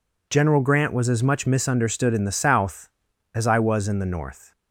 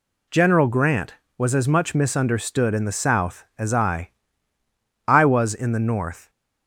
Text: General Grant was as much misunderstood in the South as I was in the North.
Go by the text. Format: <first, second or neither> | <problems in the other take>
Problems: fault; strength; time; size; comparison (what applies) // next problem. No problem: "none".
first | says "I" twice; at 5.0 s